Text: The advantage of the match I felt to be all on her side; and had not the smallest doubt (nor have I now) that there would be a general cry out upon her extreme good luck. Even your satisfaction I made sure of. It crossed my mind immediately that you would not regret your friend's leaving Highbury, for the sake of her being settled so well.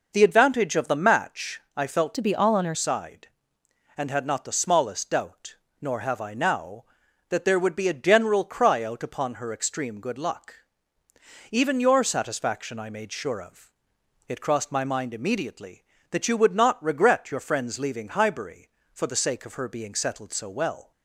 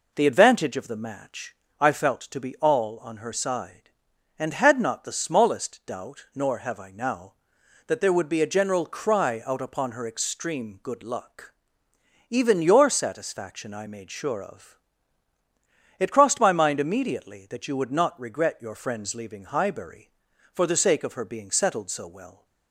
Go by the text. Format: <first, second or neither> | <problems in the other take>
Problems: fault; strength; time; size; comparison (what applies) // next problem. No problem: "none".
second | pauses between "match" and "I"; slight; at 1.5 s; 0.16 s long; slight in the second // changes voice from "to" to "her"; from 2.1 to 2.7 s; 0.6 s long